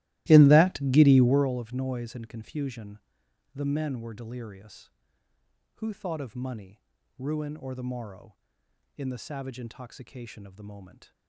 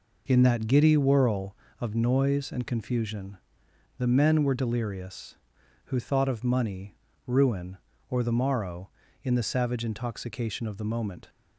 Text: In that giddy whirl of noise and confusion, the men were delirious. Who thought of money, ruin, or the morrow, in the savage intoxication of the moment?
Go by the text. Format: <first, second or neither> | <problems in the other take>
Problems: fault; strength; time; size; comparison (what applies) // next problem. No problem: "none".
second | starts louder than the rest; strong; until 1.5 s; 17 dB